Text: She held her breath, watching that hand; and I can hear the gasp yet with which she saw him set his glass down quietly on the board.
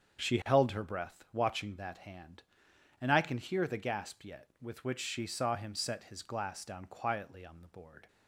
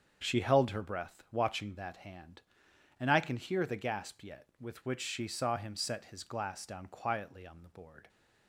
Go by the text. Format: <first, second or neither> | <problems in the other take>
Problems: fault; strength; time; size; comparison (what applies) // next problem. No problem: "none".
neither | starts louder than the rest; the same in both